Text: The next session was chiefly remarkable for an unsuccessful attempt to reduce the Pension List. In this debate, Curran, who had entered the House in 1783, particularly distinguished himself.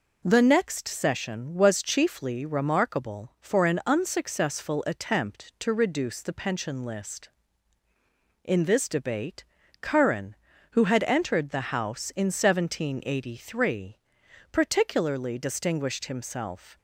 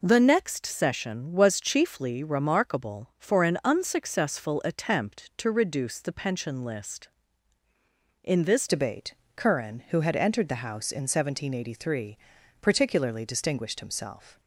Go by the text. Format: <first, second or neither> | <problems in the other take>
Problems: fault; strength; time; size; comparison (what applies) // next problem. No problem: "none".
first | changes voice at "debate"; from 8.6 s on; 5.7 s long